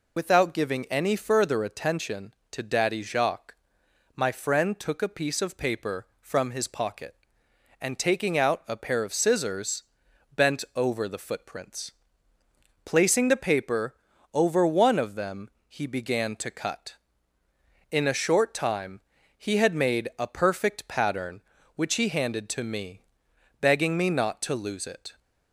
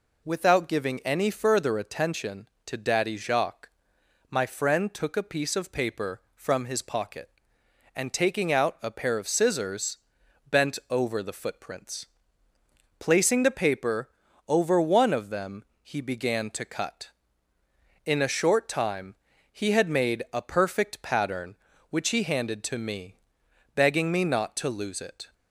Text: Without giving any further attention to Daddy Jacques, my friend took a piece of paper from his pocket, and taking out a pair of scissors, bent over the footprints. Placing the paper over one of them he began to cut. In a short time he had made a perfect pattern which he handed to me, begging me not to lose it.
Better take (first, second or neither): second